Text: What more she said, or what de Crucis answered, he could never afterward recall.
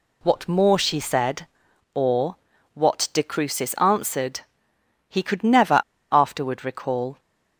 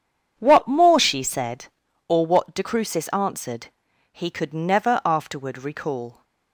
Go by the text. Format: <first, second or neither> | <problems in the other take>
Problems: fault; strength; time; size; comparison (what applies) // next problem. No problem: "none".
second | pauses between "or" and "what"; at 2.3 s; 0.38 s long // pauses between "never" and "afterward"; slight; at 5.8 s; 0.29 s long